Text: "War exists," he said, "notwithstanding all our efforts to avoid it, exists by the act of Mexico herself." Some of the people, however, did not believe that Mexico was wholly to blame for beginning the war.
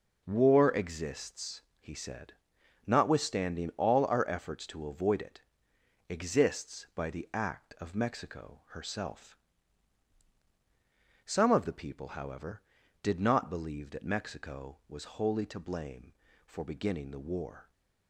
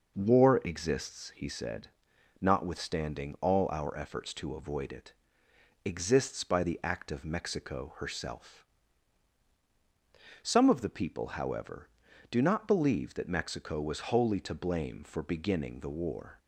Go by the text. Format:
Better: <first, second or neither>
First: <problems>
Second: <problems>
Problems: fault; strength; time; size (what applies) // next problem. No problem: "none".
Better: first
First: none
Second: says "do" for "did"; at 12.3 s